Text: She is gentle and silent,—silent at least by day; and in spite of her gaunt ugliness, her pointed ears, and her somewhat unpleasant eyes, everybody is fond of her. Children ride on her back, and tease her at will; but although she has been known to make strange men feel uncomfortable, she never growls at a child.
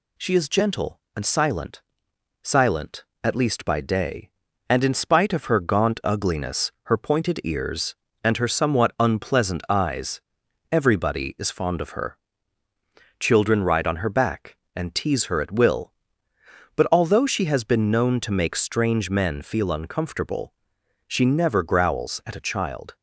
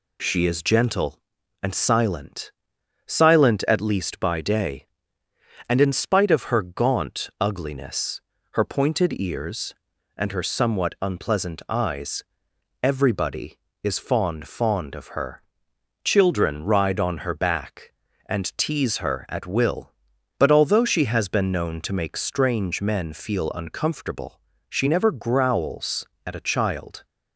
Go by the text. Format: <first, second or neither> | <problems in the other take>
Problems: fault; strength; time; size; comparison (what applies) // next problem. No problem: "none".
first | says "fond" twice; at 14.4 s